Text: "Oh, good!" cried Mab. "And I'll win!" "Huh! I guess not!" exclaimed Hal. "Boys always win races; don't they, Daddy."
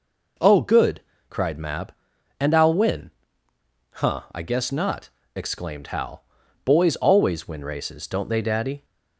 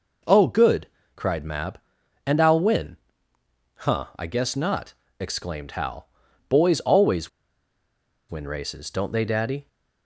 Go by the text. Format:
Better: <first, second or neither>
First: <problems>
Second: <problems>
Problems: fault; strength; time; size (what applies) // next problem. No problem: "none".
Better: first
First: none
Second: pauses between "always" and "win"; at 7.2 s; 1.0 s long